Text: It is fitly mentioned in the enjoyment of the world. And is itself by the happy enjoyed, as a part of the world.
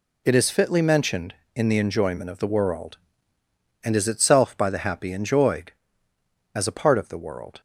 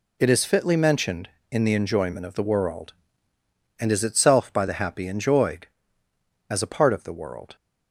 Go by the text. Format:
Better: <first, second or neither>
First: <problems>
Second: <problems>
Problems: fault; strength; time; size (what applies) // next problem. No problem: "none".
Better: neither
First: none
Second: none